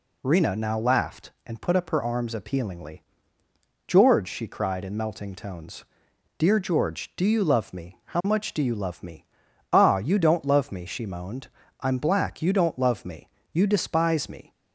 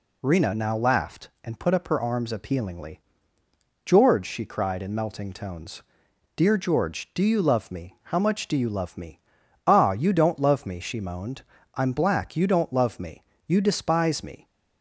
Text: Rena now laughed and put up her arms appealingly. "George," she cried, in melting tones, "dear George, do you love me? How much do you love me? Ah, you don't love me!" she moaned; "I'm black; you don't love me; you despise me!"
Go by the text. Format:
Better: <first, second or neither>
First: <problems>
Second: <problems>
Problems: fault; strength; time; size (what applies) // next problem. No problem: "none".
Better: neither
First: none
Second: none